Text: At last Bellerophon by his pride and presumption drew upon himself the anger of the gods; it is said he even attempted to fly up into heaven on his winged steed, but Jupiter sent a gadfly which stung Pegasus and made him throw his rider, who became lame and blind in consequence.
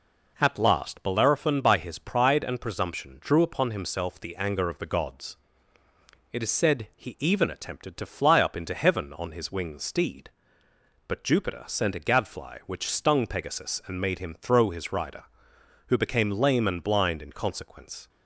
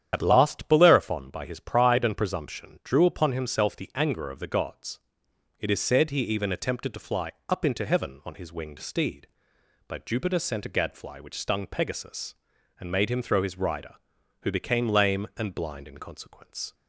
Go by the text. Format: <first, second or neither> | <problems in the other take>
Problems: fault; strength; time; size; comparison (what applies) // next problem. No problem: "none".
first | loses the start of "At"; at 0.1 s; 85 ms // starts louder than the rest; strong; until 1.1 s; 9 dB // pauses between "fly" and "up"; slight; at 7.3 s; 0.18 s long